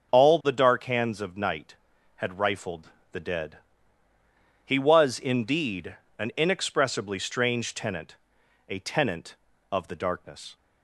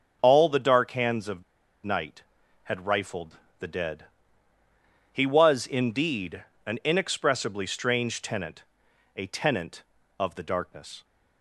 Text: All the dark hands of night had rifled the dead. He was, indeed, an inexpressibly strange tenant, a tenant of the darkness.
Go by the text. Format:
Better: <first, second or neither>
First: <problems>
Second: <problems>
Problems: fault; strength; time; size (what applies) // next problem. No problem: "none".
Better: first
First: starts louder than the rest; until 1.1 s; 6.5 dB // pauses between "rifled" and "the"; slight; at 2.8 s; 0.24 s long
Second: starts louder than the rest; until 1.2 s; 6.5 dB // pauses between "of" and "night"; at 1.4 s; 0.42 s long // pauses between "rifled" and "the"; slight; at 3.3 s; 0.24 s long